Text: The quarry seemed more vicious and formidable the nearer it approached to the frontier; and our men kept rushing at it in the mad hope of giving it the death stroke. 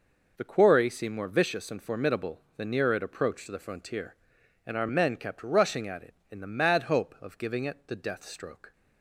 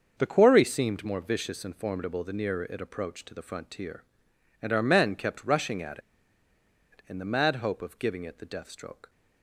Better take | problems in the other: first | starts louder than the rest; until 1.1 s; 6.5 dB // pauses between "at" and "it"; noticeable; at 5.9 s; 0.93 s long

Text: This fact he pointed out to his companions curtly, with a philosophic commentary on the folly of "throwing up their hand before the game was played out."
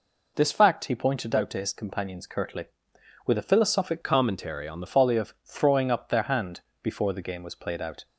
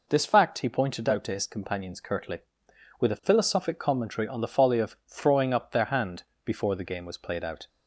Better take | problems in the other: second | changes voice from "commentary" to "the"; from 4.0 to 4.8 s; 0.8 s long // pauses between "hand" and "before"; slight; at 6.6 s; 0.20 s long; slight in the second

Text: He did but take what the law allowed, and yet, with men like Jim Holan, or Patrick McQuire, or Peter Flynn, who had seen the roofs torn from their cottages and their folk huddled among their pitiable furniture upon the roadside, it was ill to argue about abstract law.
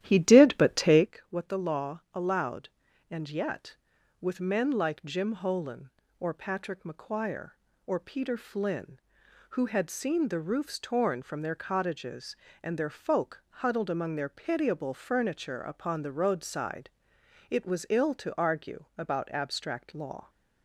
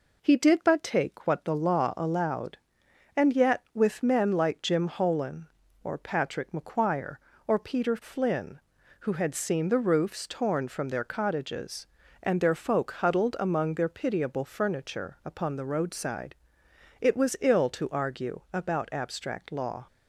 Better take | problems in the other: second | starts louder than the rest; strong; until 1.1 s; 12 dB

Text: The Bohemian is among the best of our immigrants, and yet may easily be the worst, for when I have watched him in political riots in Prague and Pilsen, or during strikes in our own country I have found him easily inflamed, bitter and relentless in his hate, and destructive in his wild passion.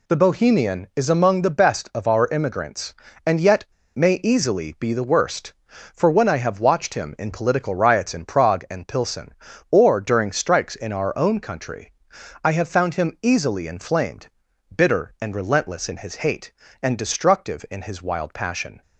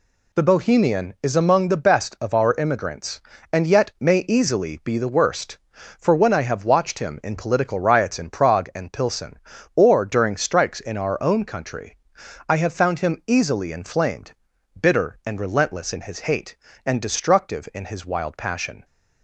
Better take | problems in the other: second | pauses between "yet" and "may"; slight; at 3.6 s; 0.29 s long // pauses between "country" and "I"; noticeable; at 11.9 s; 0.50 s long; noticeable in the second

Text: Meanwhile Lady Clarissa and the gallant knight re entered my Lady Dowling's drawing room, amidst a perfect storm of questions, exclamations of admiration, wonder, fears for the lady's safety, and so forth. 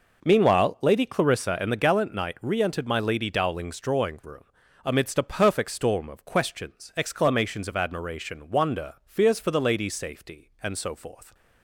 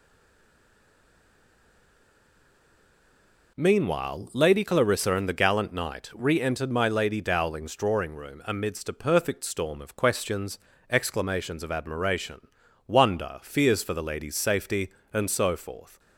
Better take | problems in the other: first | stays silent before the first word; strong; until 3.5 s; 3.5 s long

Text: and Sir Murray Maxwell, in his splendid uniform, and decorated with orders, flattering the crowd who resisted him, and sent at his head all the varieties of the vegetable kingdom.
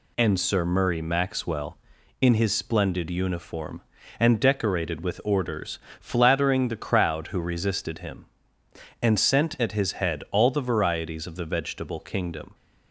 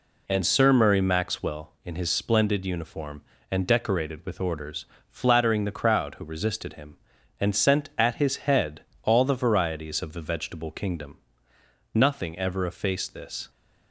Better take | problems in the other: first | pauses between "head" and "all"; slight; at 8.8 s; 0.22 s long // goes on to say "Nothing ever effaced this"; from 11.9 s on; 1.5 s long

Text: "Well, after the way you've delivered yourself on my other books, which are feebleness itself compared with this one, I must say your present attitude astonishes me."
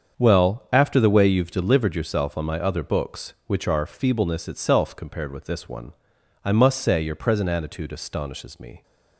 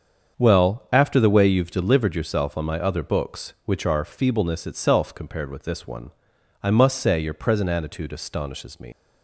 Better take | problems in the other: first | starts louder than the rest; until 1.3 s; 7 dB; also in the first // leaves "me" unfinished; at 8.9 s; 105 ms

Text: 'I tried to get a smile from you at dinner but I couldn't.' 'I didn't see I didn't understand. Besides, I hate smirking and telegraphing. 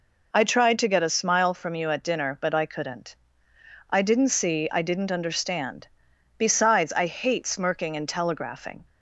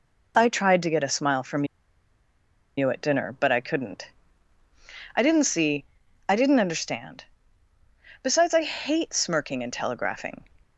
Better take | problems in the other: first | pauses between "from" and "you"; at 1.6 s; 1.1 s long // pauses between "see" and "I"; at 5.8 s; 0.44 s long

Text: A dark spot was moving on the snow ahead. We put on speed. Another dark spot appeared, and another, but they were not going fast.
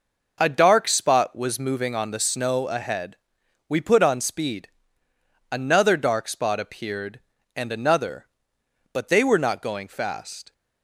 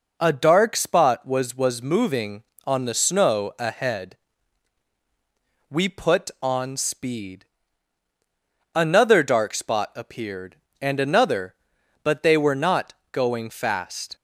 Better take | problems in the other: first | says "was" twice; at 1.5 s // pauses between "not" and "going"; slight; at 12.9 s; 0.18 s long

